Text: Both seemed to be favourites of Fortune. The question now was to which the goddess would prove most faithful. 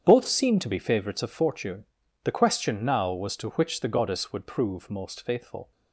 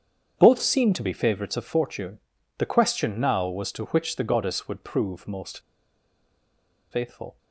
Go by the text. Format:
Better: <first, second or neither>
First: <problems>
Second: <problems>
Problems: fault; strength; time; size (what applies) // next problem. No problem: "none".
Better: first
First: starts louder than the rest; strong; until 1.0 s; 8 dB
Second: starts louder than the rest; strong; until 1.3 s; 8 dB // pauses between "most" and "faithful"; strong; at 5.6 s; 1.3 s long